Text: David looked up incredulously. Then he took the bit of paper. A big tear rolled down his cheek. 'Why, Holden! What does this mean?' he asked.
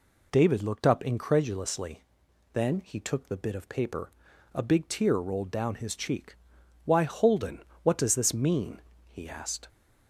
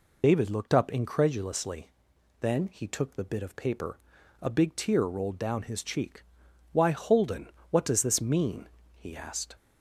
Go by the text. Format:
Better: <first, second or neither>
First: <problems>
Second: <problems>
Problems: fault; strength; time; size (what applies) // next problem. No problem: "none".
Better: first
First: none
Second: loses the start of "David"; at 0.2 s; 45 ms